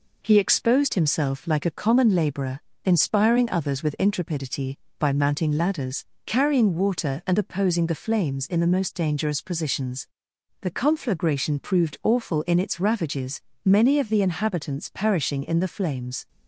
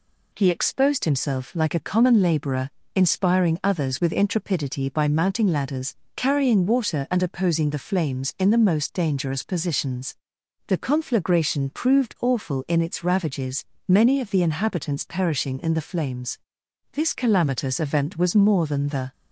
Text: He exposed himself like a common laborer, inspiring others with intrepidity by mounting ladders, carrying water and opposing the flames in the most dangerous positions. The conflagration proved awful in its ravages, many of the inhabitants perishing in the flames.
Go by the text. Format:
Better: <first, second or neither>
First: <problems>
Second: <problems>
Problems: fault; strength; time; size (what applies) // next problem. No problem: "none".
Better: first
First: none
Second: goes on to say "This calamitous event was more than the"; strong; from 16.9 s on; 2.1 s long